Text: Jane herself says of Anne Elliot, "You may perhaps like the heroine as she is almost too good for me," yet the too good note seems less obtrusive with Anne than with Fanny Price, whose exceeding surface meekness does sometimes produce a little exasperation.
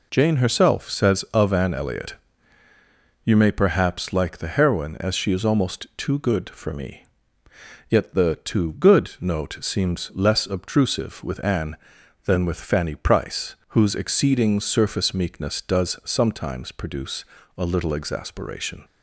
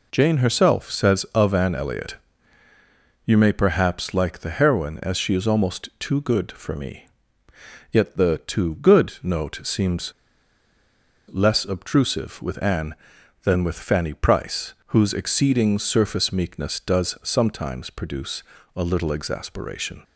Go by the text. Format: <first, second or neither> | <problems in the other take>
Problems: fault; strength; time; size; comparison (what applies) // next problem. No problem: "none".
first | pauses between "seems" and "less"; at 10.1 s; 1.1 s long // pauses between "produce" and "a"; slight; at 18.4 s; 0.34 s long; slight in the first